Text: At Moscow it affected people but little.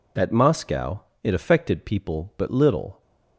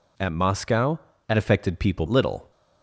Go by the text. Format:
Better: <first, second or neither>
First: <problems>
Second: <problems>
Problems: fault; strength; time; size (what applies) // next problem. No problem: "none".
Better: first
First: pauses between "Moscow" and "it"; slight; at 1.0 s; 0.20 s long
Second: pauses between "Moscow" and "it"; slight; at 0.9 s; 0.30 s long // skips "but"; at 2.0 s